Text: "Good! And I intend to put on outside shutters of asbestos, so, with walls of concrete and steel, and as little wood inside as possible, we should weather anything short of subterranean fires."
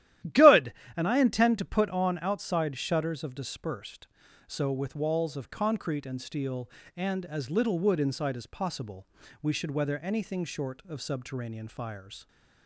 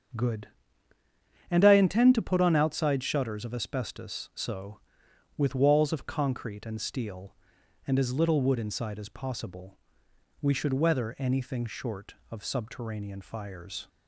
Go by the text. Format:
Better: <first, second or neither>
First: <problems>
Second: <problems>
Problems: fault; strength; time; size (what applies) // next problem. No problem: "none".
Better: second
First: starts louder than the rest; strong; until 1.5 s; 13 dB // says "dispersed" for "asbestos"; at 3.3 s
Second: starts louder than the rest; strong; until 2.1 s; 7 dB